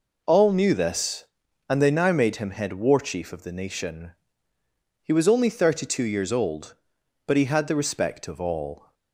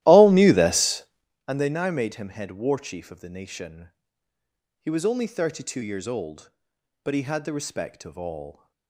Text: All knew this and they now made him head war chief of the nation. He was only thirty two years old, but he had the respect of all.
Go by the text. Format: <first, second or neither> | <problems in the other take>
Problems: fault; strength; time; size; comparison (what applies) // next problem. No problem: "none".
first | starts louder than the rest; strong; until 1.3 s; 15 dB